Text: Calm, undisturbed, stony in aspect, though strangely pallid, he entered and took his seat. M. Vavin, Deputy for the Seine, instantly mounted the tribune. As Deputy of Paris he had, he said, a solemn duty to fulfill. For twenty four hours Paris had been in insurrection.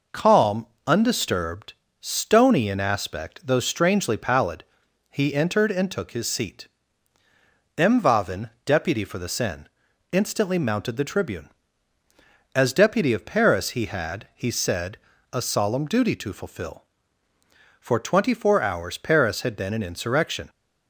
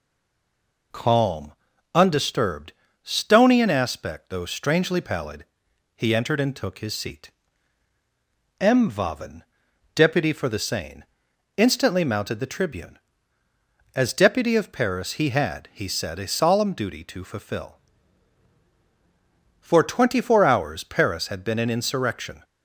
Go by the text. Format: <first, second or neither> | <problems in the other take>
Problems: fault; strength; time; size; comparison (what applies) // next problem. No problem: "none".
first | stays silent before the first word; slight; until 0.9 s; 0.9 s long